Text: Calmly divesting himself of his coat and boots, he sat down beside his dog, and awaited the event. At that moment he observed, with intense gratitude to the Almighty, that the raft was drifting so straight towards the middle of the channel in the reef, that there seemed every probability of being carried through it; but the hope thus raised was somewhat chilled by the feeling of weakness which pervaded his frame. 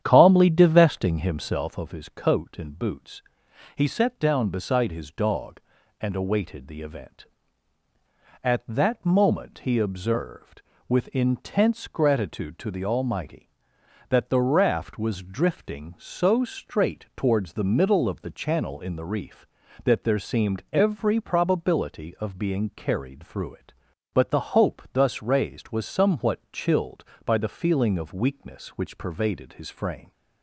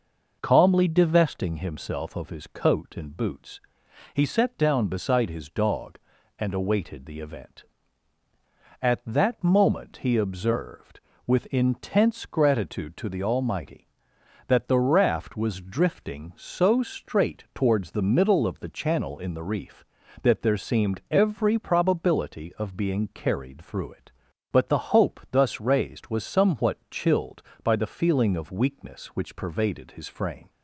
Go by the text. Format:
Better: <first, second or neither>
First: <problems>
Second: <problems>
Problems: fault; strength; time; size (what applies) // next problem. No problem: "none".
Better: second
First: starts louder than the rest; strong; until 1.8 s; 9.5 dB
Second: none